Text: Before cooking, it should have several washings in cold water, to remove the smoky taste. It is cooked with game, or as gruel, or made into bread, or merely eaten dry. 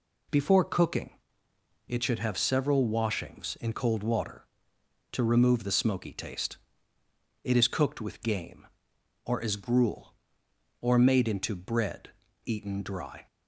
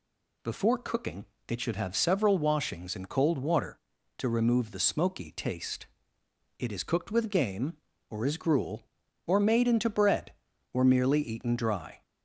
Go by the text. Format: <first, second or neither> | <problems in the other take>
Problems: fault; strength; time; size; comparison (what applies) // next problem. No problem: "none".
second | skips "or merely"; at 12.2 s